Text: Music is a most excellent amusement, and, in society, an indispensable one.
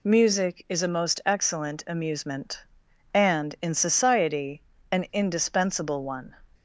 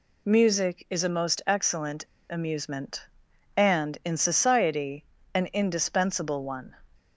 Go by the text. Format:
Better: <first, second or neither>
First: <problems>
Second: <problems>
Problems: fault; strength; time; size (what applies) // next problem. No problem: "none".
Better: first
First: none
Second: pauses between "excellent" and "amusement"; slight; at 2.0 s; 0.24 s long